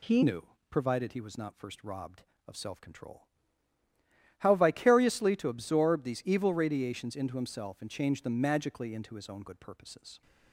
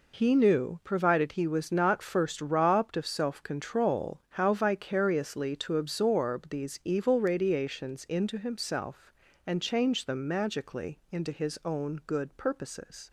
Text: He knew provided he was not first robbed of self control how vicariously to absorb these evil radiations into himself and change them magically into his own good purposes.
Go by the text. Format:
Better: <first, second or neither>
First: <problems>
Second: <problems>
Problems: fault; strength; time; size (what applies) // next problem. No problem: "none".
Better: second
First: changes voice at "knew"; from 0.2 s on; 10.0 s long // pauses between "knew" and "provided"; slight; at 0.4 s; 0.24 s long // pauses between "control" and "how"; at 3.2 s; 1.1 s long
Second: none